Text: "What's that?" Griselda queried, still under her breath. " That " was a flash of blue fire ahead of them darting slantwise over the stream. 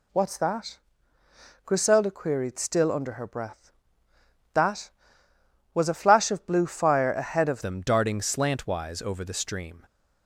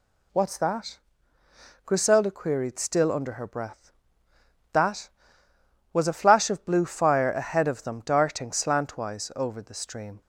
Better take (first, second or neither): second